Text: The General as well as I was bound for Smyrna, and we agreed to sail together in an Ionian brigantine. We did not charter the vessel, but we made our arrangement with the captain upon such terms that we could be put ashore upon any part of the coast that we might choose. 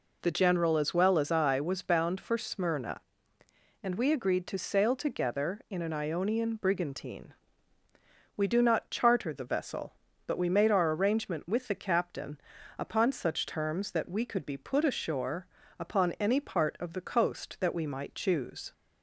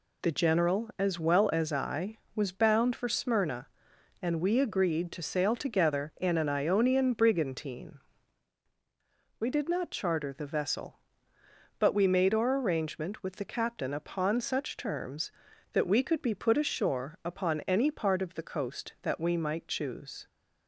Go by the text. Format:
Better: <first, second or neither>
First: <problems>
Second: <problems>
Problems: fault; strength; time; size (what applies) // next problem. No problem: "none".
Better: second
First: says "do" for "did"; at 8.4 s // pauses between "captain" and "upon"; at 12.3 s; 0.40 s long // pauses between "ashore" and "upon"; slight; at 15.4 s; 0.32 s long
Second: none